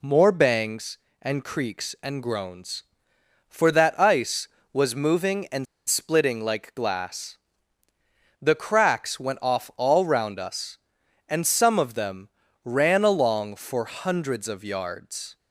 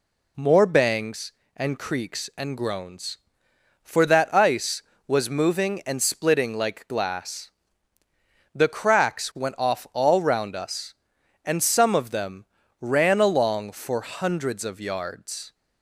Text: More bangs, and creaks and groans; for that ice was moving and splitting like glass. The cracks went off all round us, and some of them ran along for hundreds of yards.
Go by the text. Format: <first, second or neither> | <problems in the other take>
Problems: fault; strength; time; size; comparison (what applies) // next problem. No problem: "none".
second | pauses between "and" and "splitting"; slight; at 5.6 s; 0.24 s long // pauses between "them" and "ran"; slight; at 12.2 s; 0.34 s long; slight in the second